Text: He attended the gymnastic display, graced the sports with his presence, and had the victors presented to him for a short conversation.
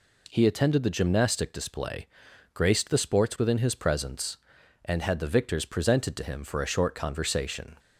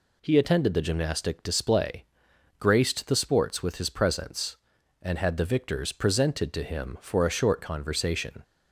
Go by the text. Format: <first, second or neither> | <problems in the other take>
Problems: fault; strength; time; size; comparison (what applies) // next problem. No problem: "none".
second | says "within" for "with"; at 3.3 s